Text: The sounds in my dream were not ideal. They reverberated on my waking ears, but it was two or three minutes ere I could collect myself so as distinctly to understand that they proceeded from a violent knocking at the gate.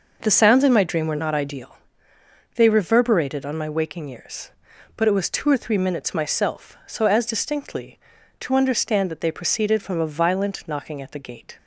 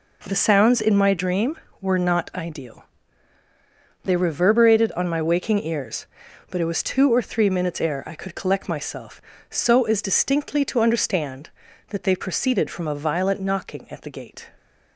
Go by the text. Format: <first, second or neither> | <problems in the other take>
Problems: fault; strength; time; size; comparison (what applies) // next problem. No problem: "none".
second | skips "ere I could collect"; at 6.1 s